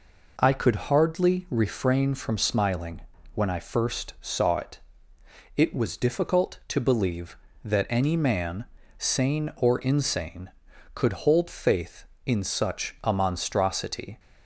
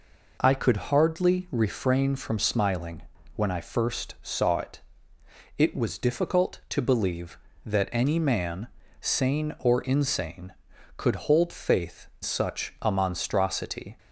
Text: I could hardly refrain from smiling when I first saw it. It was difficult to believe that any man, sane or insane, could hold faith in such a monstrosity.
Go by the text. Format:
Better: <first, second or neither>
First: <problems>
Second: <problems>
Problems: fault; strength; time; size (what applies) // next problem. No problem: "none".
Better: first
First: pauses between "smiling" and "when"; slight; at 3.0 s; 0.34 s long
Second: pauses between "smiling" and "when"; slight; at 3.0 s; 0.34 s long // skips "in"; at 12.1 s